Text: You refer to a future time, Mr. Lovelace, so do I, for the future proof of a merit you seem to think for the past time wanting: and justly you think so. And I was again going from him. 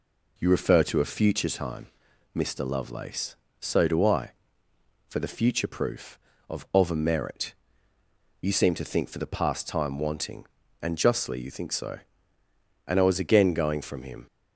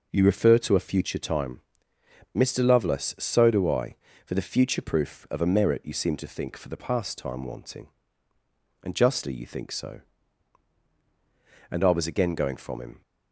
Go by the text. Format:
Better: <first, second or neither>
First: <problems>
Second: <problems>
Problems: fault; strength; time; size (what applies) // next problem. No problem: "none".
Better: second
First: says "of" twice; at 6.7 s // pauses between "merit" and "you"; noticeable; at 7.5 s; 0.86 s long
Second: none